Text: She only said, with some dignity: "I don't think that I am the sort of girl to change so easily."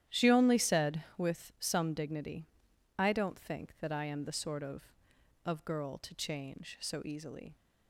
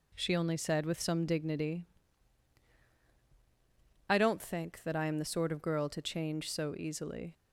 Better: second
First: starts louder than the rest; strong; until 1.2 s; 11 dB // says "of" twice; at 5.4 s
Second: none

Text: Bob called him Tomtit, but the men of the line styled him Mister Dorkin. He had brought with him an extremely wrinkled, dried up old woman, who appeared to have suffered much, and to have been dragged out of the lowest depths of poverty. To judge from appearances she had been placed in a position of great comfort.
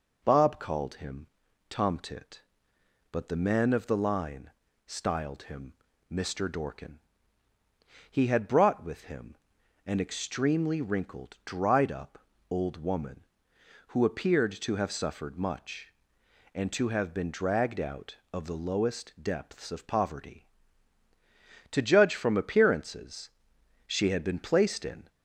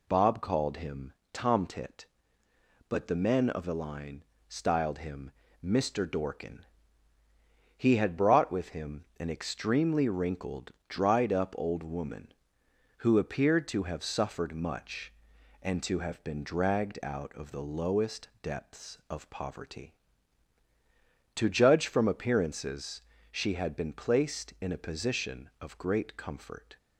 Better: second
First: pauses between "him" and "Tomtit"; at 1.2 s; 0.44 s long // pauses between "line" and "styled"; slight; at 4.5 s; 0.36 s long // pauses between "him" and "Mister"; at 5.7 s; 0.38 s long // pauses between "him" and "an"; noticeable; at 9.3 s; 0.52 s long // pauses between "up" and "old"; slight; at 12.1 s; 0.32 s long // pauses between "appearances" and "she"; noticeable; at 23.3 s; 0.56 s long // stops before "a position of great comfort"; at 25.0 s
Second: pauses between "him" and "Tomtit"; slight; at 1.1 s; 0.20 s long // pauses between "line" and "styled"; slight; at 4.2 s; 0.26 s long // pauses between "him" and "Mister"; slight; at 5.3 s; 0.32 s long // pauses between "appearances" and "she"; slight; at 23.0 s; 0.30 s long

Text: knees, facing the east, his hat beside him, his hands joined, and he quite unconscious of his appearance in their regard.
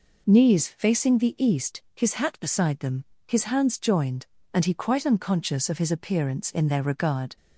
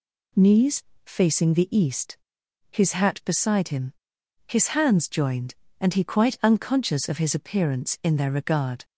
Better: second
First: says "them" for "him"; at 2.7 s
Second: none

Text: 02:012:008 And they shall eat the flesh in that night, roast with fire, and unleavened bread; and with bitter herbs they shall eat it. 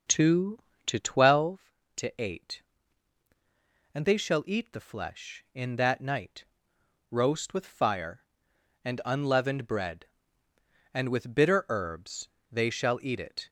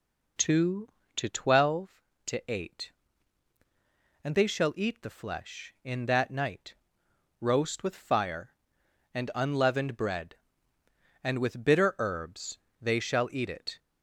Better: second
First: starts louder than the rest; until 1.5 s; 6.5 dB // pauses between "herbs" and "they"; slight; at 12.2 s; 0.24 s long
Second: pauses between "herbs" and "they"; slight; at 12.5 s; 0.24 s long

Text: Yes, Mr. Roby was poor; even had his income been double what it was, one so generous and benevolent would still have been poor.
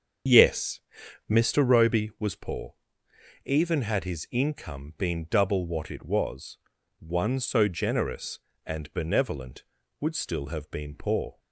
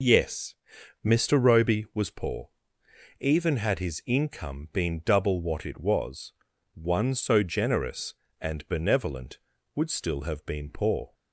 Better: second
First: starts louder than the rest; strong; until 1.5 s; 7.5 dB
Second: none

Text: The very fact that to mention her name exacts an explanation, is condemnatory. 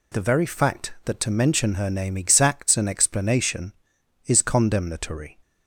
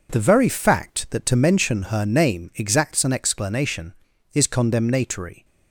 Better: neither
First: none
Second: none

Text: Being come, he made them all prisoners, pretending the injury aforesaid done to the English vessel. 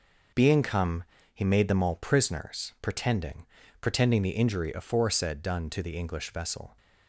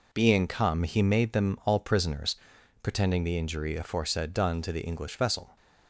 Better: second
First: says "pretending" twice; at 3.8 s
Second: none

